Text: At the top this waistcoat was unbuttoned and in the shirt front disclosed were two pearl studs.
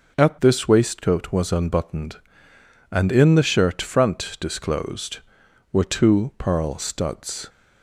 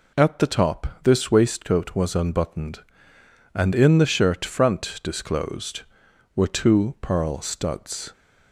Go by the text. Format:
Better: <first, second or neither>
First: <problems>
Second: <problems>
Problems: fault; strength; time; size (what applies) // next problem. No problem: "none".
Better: second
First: skips "the top"; at 0.3 s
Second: none